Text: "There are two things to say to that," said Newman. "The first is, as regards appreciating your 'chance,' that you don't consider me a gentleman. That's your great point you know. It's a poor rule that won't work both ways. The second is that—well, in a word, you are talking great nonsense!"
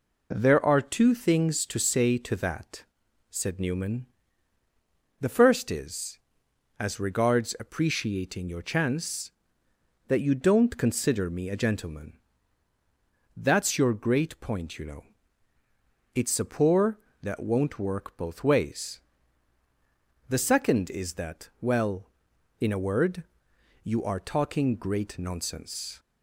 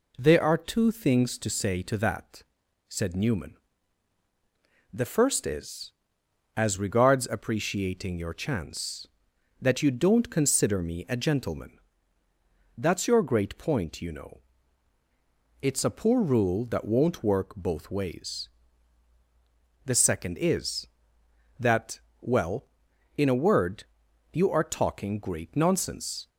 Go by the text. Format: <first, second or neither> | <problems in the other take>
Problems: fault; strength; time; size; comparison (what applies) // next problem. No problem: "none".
second | skips "rule"; at 17.0 s